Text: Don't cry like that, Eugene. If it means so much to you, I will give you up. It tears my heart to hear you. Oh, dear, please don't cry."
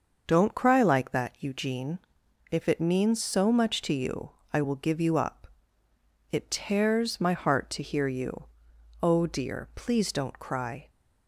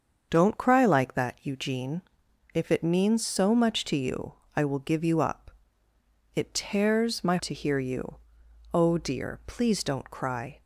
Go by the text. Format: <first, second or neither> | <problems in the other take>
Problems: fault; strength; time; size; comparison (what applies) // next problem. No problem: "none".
first | starts louder than the rest; until 1.3 s; 7 dB; also in the first // skips "heart"; at 7.3 s